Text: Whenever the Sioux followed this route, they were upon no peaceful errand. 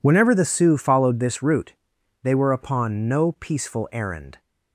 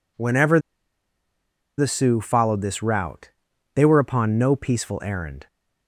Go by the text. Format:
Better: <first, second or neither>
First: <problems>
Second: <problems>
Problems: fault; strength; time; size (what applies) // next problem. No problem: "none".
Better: first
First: none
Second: pauses between "Whenever" and "the"; at 0.6 s; 1.1 s long